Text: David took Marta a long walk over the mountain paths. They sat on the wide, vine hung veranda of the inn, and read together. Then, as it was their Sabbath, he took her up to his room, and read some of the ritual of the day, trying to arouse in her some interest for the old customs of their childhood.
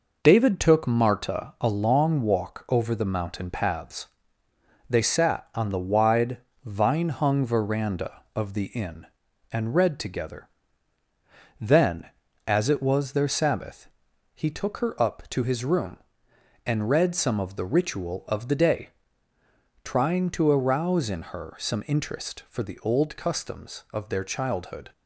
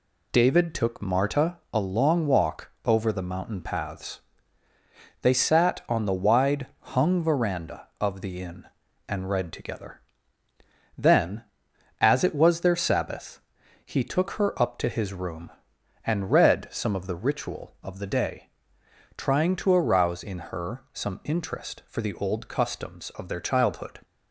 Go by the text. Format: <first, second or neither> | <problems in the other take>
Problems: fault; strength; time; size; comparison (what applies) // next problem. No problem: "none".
first | pauses between "Marta" and "a"; slight; at 1.5 s; 0.16 s long // pauses between "walk" and "over"; slight; at 2.6 s; 0.16 s long // skips "vine"; at 6.7 s